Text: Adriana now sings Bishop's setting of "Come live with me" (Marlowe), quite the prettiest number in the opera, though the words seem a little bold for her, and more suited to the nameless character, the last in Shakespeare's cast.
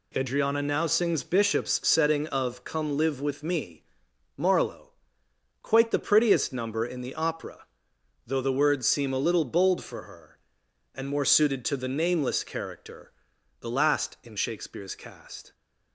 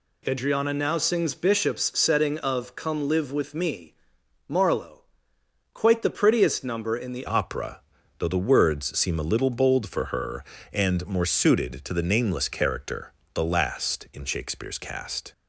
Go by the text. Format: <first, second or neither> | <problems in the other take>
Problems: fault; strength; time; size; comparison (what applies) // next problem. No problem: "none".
first | changes voice at "opera"; from 7.2 s on; 8.1 s long